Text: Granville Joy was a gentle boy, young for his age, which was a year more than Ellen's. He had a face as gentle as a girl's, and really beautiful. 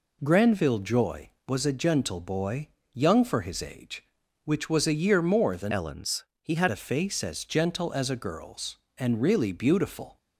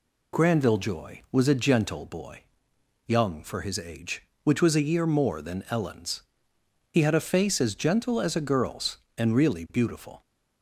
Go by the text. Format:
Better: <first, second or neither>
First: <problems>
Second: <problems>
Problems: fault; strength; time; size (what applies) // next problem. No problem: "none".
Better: second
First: changes voice from "Ellen's" to "had"; from 5.7 to 6.6 s; 0.9 s long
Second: none